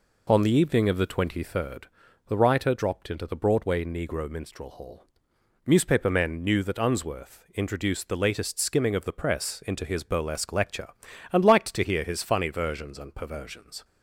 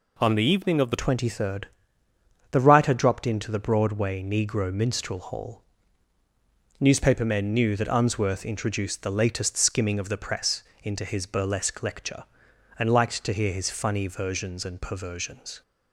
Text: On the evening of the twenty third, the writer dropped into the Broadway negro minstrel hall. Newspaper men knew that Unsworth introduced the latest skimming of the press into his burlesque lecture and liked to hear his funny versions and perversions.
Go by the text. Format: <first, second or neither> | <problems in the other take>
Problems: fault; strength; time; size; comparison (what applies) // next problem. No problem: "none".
first | changes voice at "twenty"; from 0.9 s on; 14.7 s long // pauses between "press" and "into"; slight; at 10.6 s; 0.18 s long